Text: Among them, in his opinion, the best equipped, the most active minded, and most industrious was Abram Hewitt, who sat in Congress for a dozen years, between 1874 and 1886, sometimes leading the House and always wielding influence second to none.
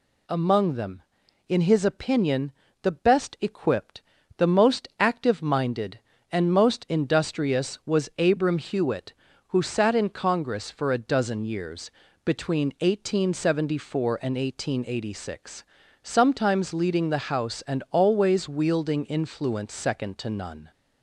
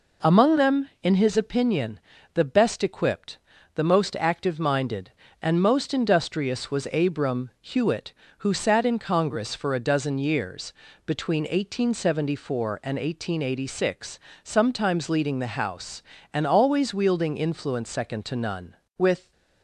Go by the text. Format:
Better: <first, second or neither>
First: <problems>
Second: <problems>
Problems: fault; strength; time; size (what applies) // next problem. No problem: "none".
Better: first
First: none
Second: goes on to say "With"; slight; from 18.9 s on; 0.32 s long